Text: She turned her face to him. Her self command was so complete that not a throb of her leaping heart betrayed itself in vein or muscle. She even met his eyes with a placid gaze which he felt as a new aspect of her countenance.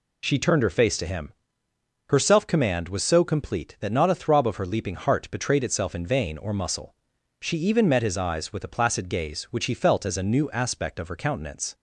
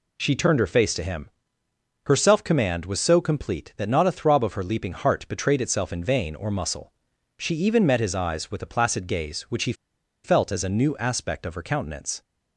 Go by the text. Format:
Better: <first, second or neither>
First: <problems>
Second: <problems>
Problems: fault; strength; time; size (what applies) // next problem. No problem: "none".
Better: first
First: none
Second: pauses between "he" and "felt"; noticeable; at 9.7 s; 0.51 s long